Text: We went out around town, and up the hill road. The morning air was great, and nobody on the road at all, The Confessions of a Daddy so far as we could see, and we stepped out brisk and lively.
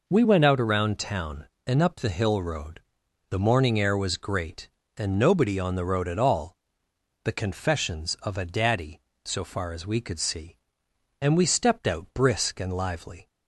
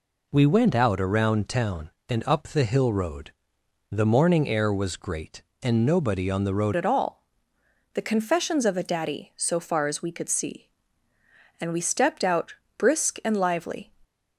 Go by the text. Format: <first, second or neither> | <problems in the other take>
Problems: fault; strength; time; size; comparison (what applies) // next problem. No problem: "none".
first | changes voice at "at"; from 6.7 s on; 7.2 s long // pauses between "out" and "brisk"; slight; at 12.5 s; 0.24 s long